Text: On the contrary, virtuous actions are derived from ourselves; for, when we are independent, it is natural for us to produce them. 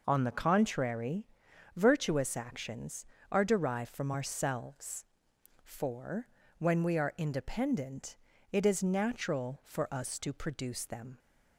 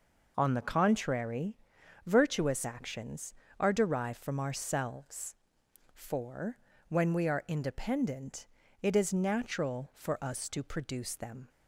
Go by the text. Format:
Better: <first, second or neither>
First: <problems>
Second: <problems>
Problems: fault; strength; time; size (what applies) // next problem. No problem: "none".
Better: neither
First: none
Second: none